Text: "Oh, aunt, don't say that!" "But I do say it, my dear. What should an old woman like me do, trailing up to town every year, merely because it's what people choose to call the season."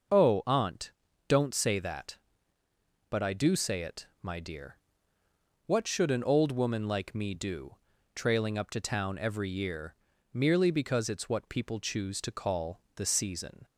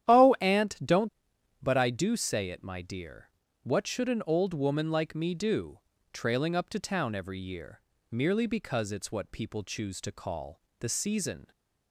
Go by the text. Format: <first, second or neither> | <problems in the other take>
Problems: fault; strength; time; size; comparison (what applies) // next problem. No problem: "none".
first | starts louder than the rest; strong; until 1.1 s; 10.5 dB; noticeable in the first // skips "say that"; at 1.3 s // pauses between "call" and "the"; slight; at 10.6 s; 0.16 s long; slight in the first